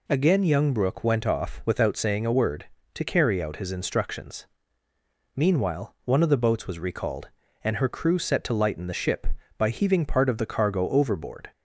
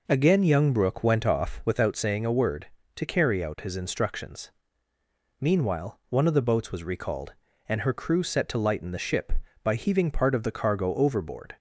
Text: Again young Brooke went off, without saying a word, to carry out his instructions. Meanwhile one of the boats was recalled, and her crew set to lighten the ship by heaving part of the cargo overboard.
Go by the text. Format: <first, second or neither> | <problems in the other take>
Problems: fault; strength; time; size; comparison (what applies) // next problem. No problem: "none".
first | starts louder than the rest; noticeable; until 1.7 s; 4.5 dB